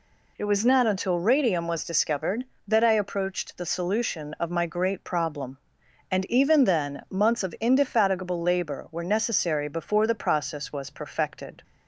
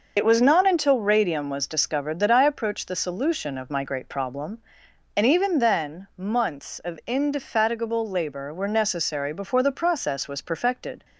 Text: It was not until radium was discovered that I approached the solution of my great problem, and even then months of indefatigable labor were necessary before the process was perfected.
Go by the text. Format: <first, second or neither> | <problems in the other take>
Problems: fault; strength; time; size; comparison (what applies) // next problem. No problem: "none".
first | loses the start of "It"; at 0.1 s; 60 ms